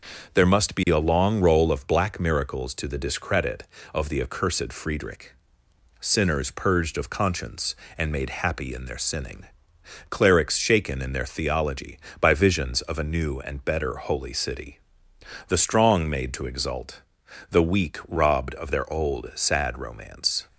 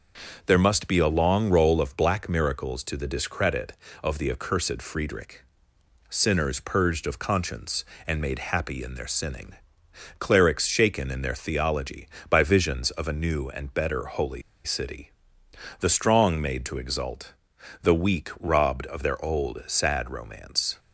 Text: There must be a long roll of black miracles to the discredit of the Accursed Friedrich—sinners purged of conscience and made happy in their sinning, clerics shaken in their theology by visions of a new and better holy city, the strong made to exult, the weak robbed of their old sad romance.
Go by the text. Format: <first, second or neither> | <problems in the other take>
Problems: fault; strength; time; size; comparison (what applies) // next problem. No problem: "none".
first | starts louder than the rest; until 1.4 s; 6.5 dB // pauses between "holy" and "city"; slight; at 14.4 s; 0.23 s long